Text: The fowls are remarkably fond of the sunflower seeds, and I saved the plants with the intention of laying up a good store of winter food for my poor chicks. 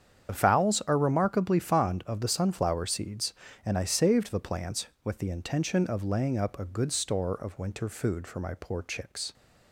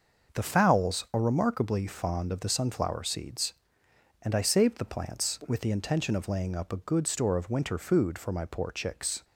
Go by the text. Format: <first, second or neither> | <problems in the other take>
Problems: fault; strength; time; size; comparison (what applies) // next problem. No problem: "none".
second | loses the start of "The"; at 0.2 s; 40 ms // starts louder than the rest; strong; until 1.3 s; 8 dB; noticeable in the second